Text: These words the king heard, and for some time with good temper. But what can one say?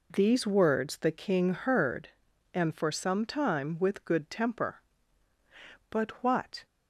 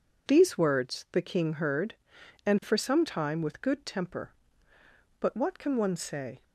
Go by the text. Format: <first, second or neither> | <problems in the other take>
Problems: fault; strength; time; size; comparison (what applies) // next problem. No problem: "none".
second | stops before "can one say"; at 6.6 s